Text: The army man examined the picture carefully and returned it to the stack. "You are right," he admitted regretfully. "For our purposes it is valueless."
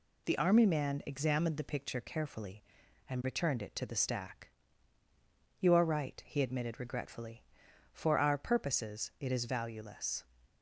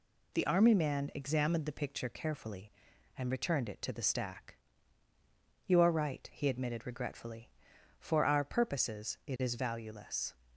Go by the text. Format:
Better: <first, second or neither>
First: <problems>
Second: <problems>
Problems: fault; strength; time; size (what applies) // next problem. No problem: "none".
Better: neither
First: none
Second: none